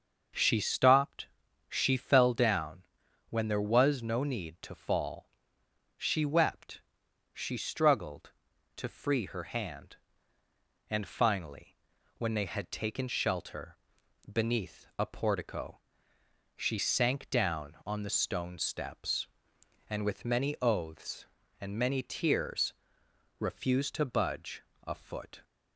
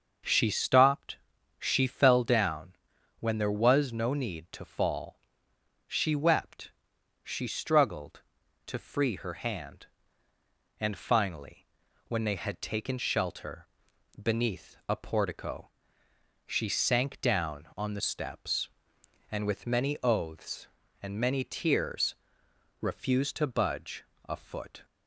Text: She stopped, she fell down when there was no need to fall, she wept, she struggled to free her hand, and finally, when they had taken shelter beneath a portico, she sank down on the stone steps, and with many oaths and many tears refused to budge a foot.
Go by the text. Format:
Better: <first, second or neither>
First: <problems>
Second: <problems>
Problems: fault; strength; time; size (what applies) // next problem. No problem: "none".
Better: first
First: starts louder than the rest; until 1.7 s; 6.5 dB // pauses between "down" and "when"; at 2.8 s; 0.44 s long // pauses between "shelter" and "beneath"; noticeable; at 13.7 s; 0.54 s long // pauses between "tears" and "refused"; noticeable; at 22.7 s; 0.64 s long // pauses between "budge" and "a"; slight; at 24.6 s; 0.24 s long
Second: starts louder than the rest; until 1.6 s; 6.5 dB // pauses between "down" and "when"; at 2.7 s; 0.44 s long // pauses between "shelter" and "beneath"; noticeable; at 13.6 s; 0.54 s long // skips "stone"; at 17.9 s // pauses between "tears" and "refused"; noticeable; at 22.1 s; 0.64 s long // pauses between "budge" and "a"; slight; at 24.0 s; 0.24 s long